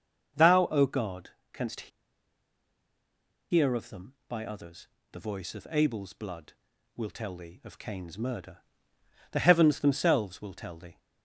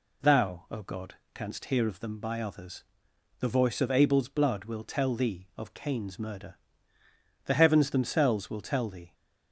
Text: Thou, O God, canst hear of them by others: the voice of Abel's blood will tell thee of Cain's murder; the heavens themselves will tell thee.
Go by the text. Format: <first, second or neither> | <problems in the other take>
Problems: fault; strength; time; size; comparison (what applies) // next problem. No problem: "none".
second | starts louder than the rest; until 1.5 s; 6.5 dB // pauses between "canst" and "hear"; strong; at 1.9 s; 1.6 s long